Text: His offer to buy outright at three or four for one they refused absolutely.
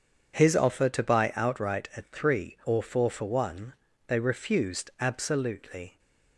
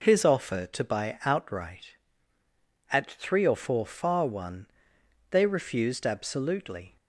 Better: first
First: pauses between "one" and "they"; slight; at 3.7 s; 0.34 s long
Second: says "far" for "for"; at 3.8 s // pauses between "one" and "they"; noticeable; at 4.6 s; 0.64 s long

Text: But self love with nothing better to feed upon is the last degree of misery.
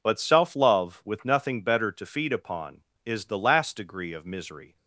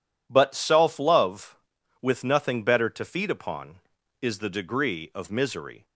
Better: first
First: none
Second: skips "last"; at 4.4 s

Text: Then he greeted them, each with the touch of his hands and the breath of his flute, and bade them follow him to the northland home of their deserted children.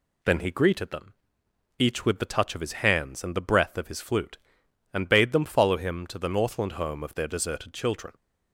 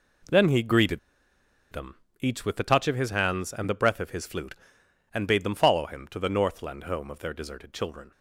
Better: first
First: none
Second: pauses between "greeted" and "them"; noticeable; at 0.9 s; 0.73 s long

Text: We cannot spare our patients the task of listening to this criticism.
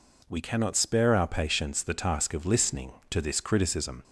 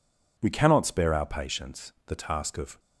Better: first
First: none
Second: stops before "listening to this criticism"; at 2.7 s

